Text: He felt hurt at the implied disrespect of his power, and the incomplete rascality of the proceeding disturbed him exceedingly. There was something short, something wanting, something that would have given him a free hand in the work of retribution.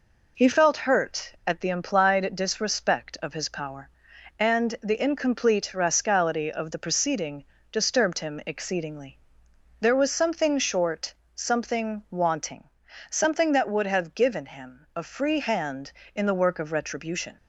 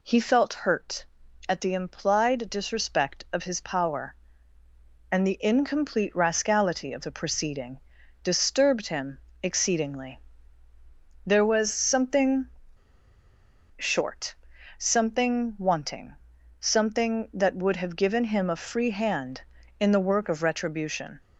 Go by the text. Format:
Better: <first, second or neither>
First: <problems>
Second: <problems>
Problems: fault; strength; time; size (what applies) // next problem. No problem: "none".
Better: first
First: pauses between "proceeding" and "disturbed"; slight; at 7.4 s; 0.26 s long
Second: pauses between "proceeding" and "disturbed"; at 7.7 s; 0.44 s long // pauses between "him" and "exceedingly"; slight; at 9.1 s; 0.24 s long // pauses between "something" and "short"; strong; at 12.4 s; 1.2 s long